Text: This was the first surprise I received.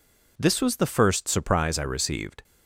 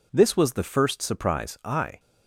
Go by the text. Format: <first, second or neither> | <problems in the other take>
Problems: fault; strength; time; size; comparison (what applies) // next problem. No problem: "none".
first | stops before "received"; at 1.9 s